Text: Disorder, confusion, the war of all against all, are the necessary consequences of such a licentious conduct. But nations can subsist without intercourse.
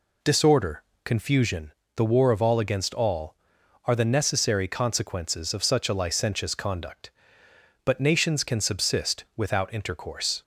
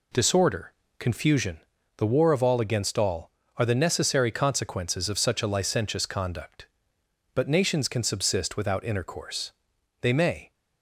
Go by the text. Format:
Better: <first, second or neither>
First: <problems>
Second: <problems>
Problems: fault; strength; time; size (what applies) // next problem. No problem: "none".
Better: first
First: none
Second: goes on to say "They may"; from 10.0 s on; 0.50 s long